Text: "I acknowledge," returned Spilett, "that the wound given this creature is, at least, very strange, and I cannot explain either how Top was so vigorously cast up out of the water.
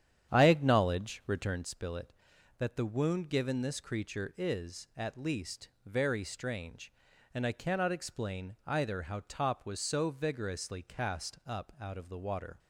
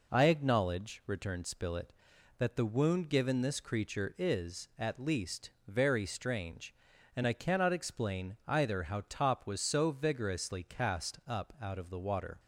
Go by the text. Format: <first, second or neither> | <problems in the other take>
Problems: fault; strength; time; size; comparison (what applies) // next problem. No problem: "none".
second | starts louder than the rest; strong; until 1.7 s; 9.5 dB